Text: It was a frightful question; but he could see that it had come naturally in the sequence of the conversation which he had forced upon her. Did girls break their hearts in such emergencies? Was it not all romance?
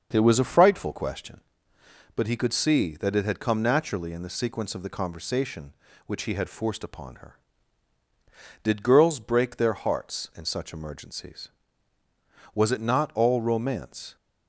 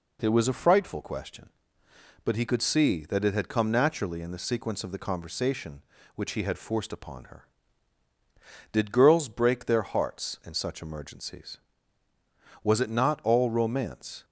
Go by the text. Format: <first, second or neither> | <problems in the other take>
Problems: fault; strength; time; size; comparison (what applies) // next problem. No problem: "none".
second | starts louder than the rest; until 1.5 s; 6.5 dB